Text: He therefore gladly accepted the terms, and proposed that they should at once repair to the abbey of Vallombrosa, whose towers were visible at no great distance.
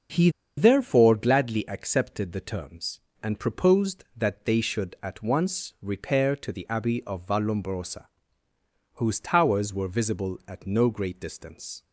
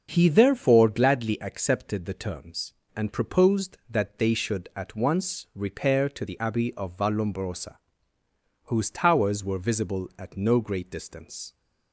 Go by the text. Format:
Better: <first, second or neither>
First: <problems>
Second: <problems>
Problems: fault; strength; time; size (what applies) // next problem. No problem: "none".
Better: second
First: starts louder than the rest; until 1.4 s; 6.5 dB // pauses between "He" and "therefore"; slight; at 0.2 s; 0.28 s long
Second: starts louder than the rest; until 1.1 s; 6.5 dB